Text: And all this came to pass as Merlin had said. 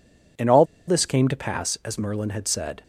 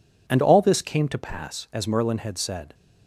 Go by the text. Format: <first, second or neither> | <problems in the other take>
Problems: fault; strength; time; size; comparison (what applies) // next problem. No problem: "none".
second | pauses between "all" and "this"; slight; at 0.6 s; 0.22 s long